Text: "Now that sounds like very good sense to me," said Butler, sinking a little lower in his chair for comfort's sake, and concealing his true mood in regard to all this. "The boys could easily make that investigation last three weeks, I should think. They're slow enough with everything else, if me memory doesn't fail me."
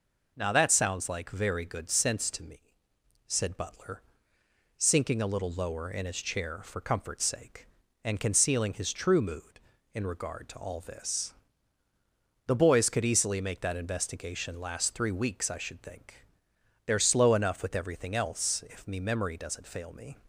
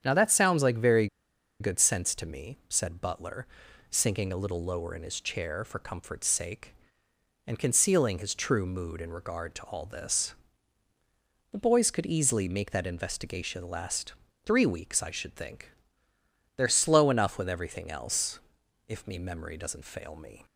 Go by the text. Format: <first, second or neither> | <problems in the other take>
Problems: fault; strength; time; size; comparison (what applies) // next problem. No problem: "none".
first | starts louder than the rest; strong; until 1.0 s; 8.5 dB // pauses between "very" and "good"; noticeable; at 1.0 s; 0.52 s long // pauses between "last" and "three"; slight; at 14.1 s; 0.32 s long